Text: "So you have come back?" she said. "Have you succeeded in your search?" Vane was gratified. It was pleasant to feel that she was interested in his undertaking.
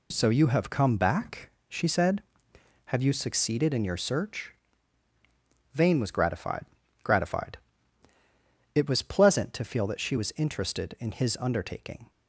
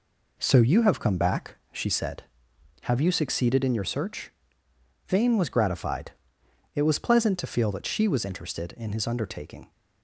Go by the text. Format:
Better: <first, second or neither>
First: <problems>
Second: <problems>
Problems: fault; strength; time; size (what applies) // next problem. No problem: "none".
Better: second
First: says "gratified" twice; at 7.0 s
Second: none